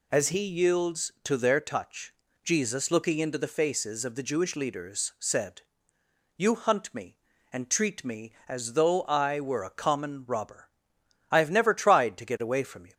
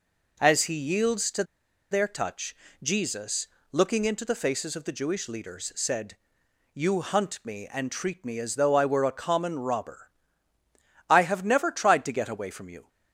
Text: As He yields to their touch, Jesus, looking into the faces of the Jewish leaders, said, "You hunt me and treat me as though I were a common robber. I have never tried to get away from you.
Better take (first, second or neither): first